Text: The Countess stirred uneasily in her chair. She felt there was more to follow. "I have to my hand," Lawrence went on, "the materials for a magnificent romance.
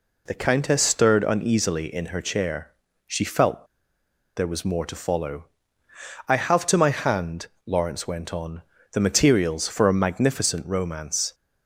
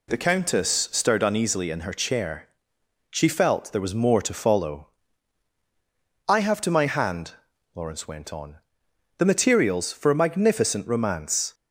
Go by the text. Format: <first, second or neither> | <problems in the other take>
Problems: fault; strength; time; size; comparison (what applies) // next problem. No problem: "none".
second | pauses between "felt" and "there"; noticeable; at 3.6 s; 0.69 s long